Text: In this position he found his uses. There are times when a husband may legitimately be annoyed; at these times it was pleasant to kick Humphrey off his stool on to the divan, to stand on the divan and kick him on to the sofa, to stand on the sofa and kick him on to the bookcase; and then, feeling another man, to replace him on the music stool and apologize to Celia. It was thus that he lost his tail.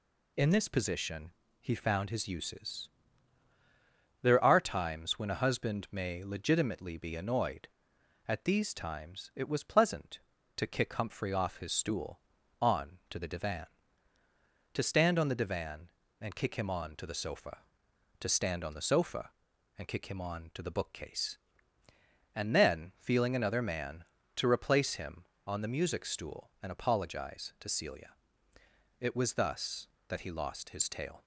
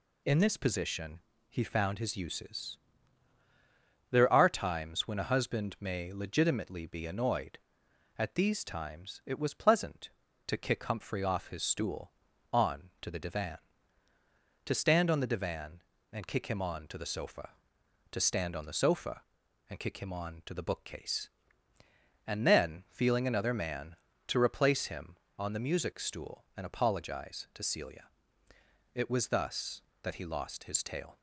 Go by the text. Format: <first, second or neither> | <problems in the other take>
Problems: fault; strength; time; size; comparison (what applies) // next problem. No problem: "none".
neither | pauses between "position" and "he"; slight; the same in both